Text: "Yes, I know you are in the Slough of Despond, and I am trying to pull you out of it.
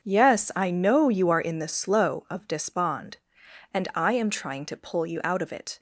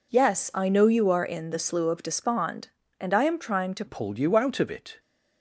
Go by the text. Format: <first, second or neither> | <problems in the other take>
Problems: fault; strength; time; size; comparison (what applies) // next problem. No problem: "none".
first | changes voice at "pull"; from 3.8 s on; 1.1 s long